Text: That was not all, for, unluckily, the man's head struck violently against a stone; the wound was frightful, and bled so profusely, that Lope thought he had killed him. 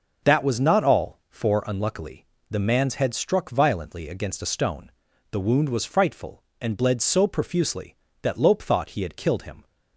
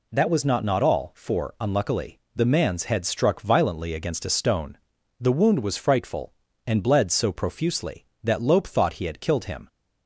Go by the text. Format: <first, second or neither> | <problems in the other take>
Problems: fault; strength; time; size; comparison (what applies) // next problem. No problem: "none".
first | says "not" twice; at 0.6 s